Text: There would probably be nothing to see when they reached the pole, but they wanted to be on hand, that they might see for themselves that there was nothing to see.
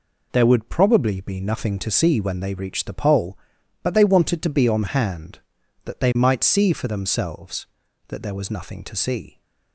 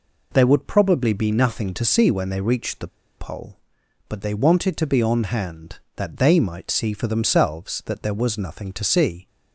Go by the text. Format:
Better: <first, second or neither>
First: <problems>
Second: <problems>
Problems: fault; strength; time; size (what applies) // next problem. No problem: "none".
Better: first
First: none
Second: pauses between "the" and "pole"; slight; at 2.8 s; 0.31 s long